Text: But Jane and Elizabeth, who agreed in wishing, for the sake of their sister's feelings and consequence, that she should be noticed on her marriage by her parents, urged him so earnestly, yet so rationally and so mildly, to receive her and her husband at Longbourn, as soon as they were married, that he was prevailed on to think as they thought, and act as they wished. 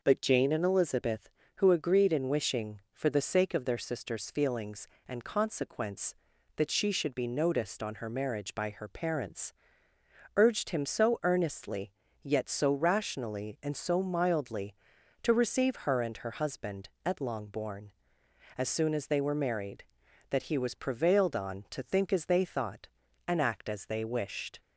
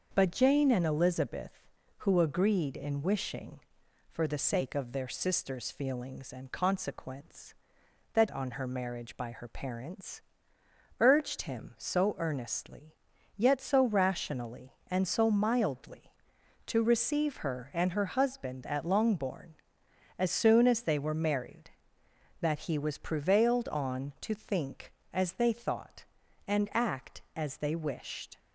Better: first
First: none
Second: starts louder than the rest; noticeable; until 1.1 s; 6 dB // skips "she should be noticed"; at 8.2 s

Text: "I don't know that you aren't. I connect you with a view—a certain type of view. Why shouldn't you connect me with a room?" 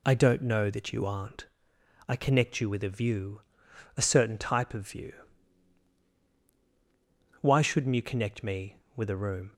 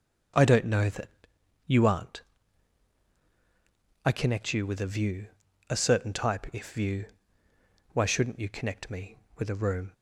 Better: first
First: none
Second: starts louder than the rest; until 1.9 s; 7 dB // pauses between "that" and "you"; noticeable; at 1.0 s; 0.58 s long // says "if" for "of"; at 6.5 s

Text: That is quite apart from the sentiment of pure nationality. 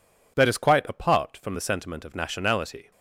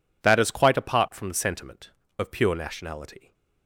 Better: second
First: skips "pure"; at 2.1 s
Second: none

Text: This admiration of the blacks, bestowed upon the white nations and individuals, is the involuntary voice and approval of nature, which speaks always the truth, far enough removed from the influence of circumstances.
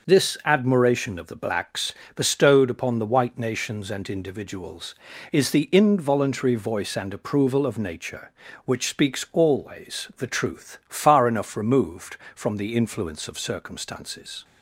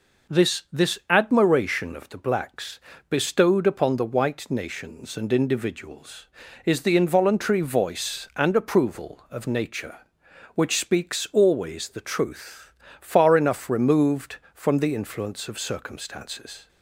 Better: first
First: none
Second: says "This" twice; at 0.7 s

